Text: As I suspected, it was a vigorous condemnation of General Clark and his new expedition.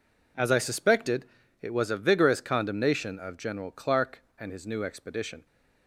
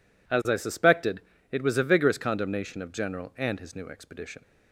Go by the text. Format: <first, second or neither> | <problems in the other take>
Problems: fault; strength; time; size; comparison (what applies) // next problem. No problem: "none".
first | skips "Clark"; at 3.3 s